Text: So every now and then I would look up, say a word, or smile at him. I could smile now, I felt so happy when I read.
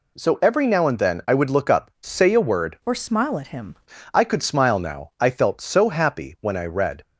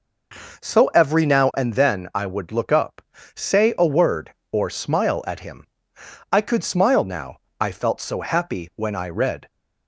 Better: second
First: changes voice from "or" to "him"; from 2.8 to 3.7 s; 0.9 s long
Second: none

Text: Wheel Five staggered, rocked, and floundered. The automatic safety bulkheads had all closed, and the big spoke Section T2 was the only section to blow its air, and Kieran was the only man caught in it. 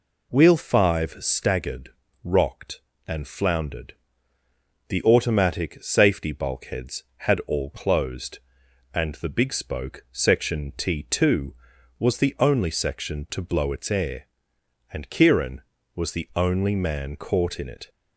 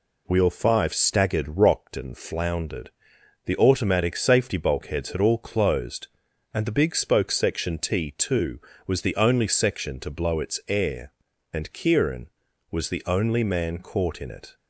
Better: neither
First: none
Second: none

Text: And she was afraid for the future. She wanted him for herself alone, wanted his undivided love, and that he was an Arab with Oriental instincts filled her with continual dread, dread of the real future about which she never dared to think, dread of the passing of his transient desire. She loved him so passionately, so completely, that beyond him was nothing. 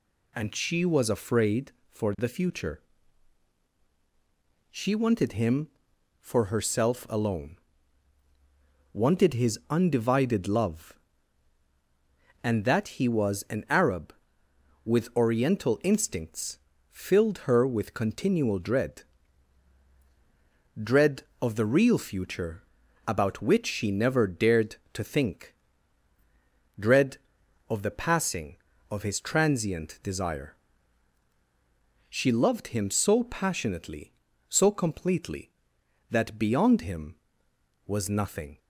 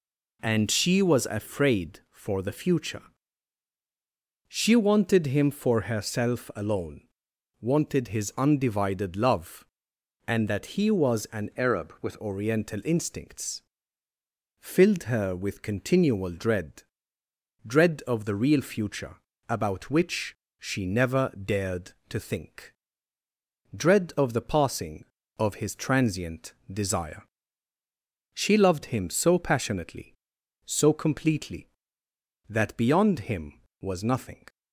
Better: first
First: pauses between "instincts" and "filled"; slight; at 16.5 s; 0.32 s long // pauses between "future" and "about"; at 22.6 s; 0.44 s long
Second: changes voice from "Arab" to "with"; from 11.5 to 12.2 s; 0.7 s long // pauses between "instincts" and "filled"; noticeable; at 13.6 s; 0.98 s long // pauses between "future" and "about"; slight; at 19.1 s; 0.34 s long // pauses between "which" and "she"; slight; at 20.3 s; 0.20 s long // pauses between "transient" and "desire"; slight; at 26.5 s; 0.18 s long

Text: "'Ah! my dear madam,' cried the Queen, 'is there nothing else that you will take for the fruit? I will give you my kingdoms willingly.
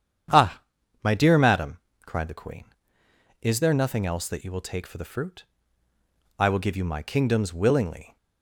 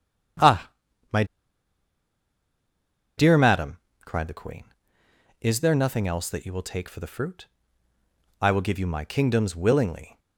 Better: first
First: starts louder than the rest; strong; until 1.7 s; 9 dB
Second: starts louder than the rest; strong; until 3.7 s; 9 dB // pauses between "my" and "dear"; strong; at 1.2 s; 1.9 s long

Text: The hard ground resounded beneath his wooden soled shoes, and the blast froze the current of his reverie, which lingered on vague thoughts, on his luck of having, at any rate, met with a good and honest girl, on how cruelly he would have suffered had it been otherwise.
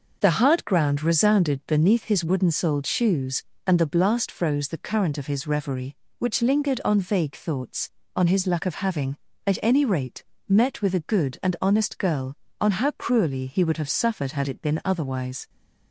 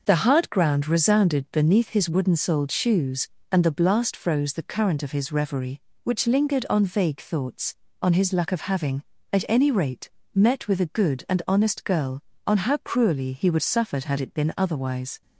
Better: first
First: none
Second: skips "have"; at 13.6 s

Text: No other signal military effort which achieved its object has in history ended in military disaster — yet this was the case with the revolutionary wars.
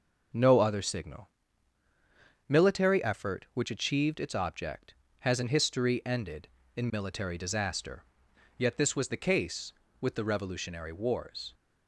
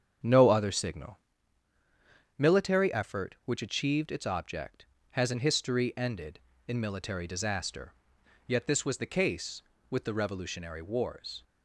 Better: first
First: pauses between "signal" and "military"; at 1.2 s; 1.2 s long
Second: starts louder than the rest; strong; until 1.4 s; 8 dB // pauses between "signal" and "military"; at 1.1 s; 1.2 s long

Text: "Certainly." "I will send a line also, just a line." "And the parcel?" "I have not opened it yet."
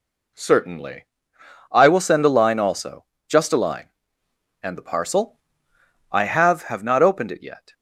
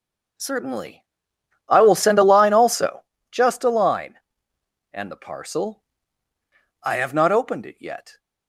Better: second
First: says "have" twice; at 6.6 s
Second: none

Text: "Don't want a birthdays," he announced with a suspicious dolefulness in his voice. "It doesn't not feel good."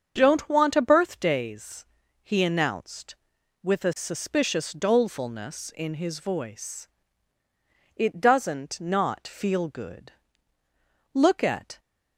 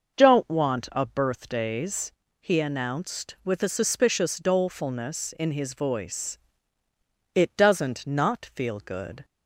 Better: second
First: starts louder than the rest; strong; until 1.1 s; 7.5 dB // goes on to say "Look at"; noticeable; from 11.1 s on; 0.66 s long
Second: none

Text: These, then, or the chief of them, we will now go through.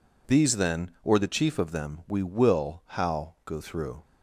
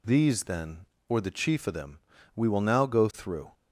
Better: second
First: says "how" for "now"; at 2.8 s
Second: none

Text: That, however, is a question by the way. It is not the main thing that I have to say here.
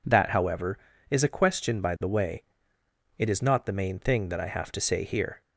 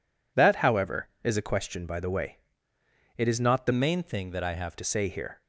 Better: first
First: none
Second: changes voice from "main" to "have"; from 3.7 to 4.7 s; 1.0 s long

